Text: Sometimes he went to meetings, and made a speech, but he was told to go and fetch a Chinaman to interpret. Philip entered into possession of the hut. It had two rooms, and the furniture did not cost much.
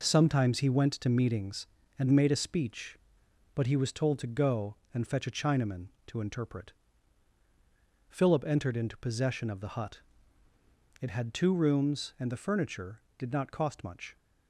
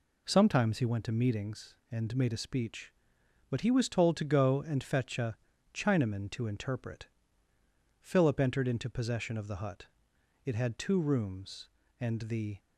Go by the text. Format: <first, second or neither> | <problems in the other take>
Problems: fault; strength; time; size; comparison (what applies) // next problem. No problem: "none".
first | pauses between "a" and "Chinaman"; slight; at 5.3 s; 0.36 s long // stops before "furniture did not cost much"; at 12.5 s